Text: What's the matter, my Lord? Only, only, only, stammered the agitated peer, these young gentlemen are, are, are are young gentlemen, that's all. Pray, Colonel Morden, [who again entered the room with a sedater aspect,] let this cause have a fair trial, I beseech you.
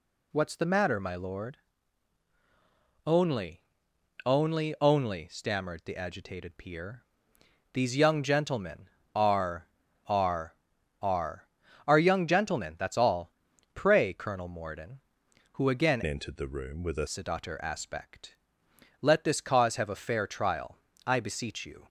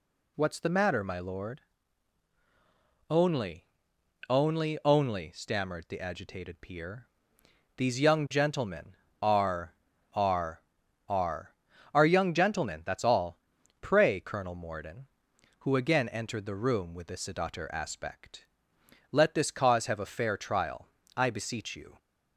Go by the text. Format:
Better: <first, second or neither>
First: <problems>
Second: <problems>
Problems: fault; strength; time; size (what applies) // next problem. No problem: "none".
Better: second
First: changes voice from "entered" to "a"; from 16.0 to 17.0 s; 1.0 s long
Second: none